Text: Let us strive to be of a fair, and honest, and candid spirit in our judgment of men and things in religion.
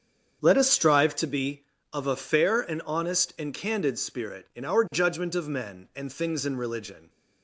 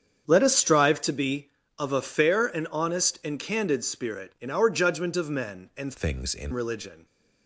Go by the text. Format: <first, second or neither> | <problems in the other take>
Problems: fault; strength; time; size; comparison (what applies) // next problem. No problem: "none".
first | starts louder than the rest; strong; until 1.3 s; 8 dB; strong in the first // changes voice from "things" to "in"; from 5.9 to 6.5 s; 0.6 s long